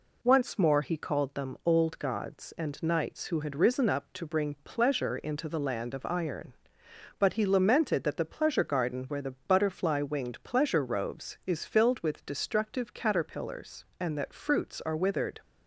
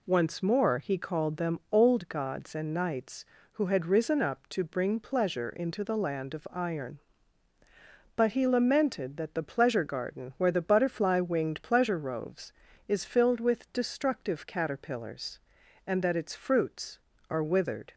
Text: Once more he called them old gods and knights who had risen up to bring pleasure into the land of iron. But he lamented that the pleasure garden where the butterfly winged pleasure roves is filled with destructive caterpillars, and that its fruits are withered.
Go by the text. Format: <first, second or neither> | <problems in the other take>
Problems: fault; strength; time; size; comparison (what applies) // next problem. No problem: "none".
second | skips "its"; at 14.3 s